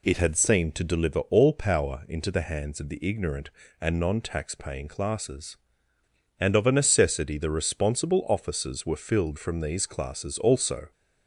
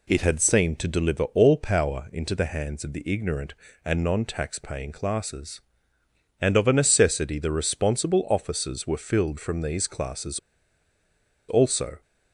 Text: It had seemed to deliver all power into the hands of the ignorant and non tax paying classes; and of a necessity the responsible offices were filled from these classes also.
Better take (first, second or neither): first